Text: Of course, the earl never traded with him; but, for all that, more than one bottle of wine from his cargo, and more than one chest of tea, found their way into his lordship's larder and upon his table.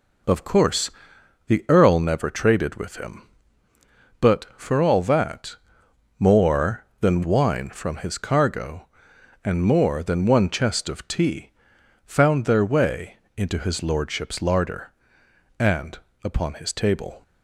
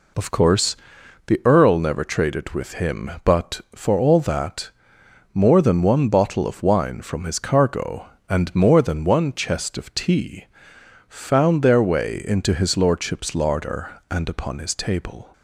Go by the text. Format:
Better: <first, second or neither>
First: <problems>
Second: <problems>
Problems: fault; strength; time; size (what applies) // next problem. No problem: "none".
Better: second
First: skips "one bottle of"; at 7.2 s // pauses between "way" and "into"; slight; at 13.1 s; 0.20 s long // pauses between "and" and "upon"; slight; at 15.9 s; 0.26 s long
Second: none